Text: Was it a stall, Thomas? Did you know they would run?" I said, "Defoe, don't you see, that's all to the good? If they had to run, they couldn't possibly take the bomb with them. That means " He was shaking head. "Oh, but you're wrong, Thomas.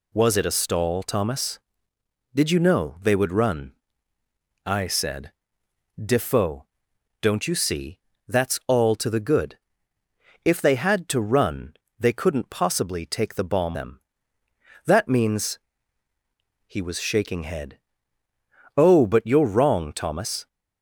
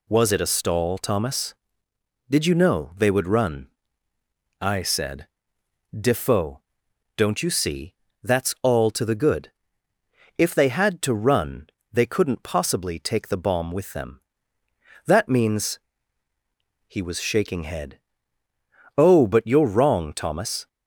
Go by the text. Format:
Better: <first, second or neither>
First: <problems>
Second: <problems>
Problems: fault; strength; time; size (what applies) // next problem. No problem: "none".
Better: second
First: skips "with"; at 13.7 s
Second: none